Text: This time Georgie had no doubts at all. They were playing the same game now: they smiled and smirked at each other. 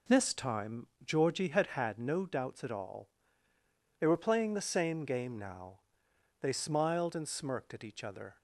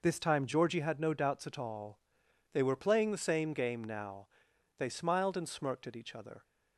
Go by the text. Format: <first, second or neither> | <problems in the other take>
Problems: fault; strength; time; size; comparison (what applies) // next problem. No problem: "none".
second | pauses between "time" and "Georgie"; slight; at 0.8 s; 0.18 s long // says "had" twice; at 1.6 s